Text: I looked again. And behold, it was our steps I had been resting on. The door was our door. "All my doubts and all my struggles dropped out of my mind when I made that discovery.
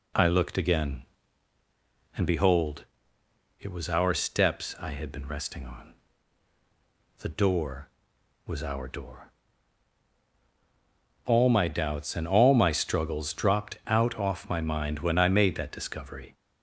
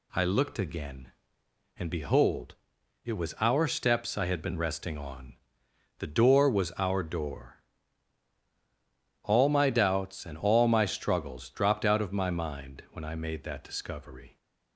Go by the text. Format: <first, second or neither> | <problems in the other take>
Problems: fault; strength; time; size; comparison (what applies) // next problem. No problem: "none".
second | says "off" for "of"; at 14.1 s